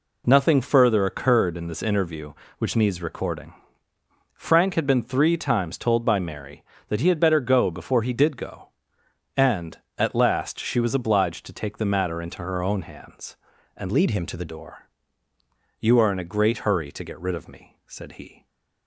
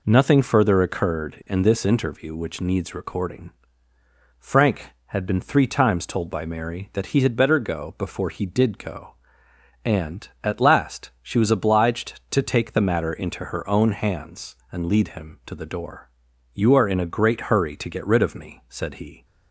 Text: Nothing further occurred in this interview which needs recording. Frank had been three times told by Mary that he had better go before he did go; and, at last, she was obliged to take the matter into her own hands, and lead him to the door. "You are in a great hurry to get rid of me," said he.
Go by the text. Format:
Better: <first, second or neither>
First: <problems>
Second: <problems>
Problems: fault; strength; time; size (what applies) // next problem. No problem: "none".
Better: second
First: changes voice from "lead" to "the"; from 13.9 to 14.4 s; 0.5 s long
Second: none